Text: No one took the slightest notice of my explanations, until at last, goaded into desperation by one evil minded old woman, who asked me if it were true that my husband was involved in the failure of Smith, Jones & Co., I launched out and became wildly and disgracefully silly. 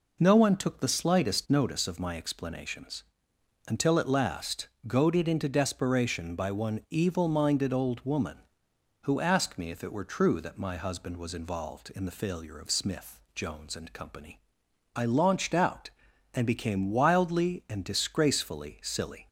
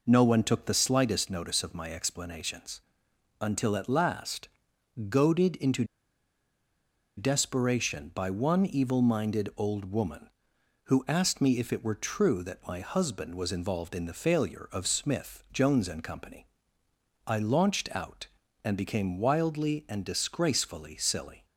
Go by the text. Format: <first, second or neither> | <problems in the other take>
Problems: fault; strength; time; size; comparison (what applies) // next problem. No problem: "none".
first | pauses between "into" and "desperation"; strong; at 5.8 s; 1.3 s long